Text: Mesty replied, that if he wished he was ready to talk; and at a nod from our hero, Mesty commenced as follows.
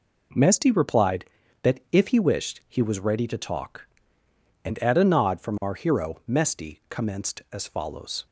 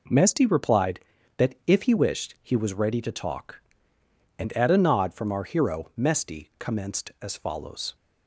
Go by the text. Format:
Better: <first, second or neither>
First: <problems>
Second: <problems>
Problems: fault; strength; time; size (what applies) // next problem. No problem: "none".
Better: neither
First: none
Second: none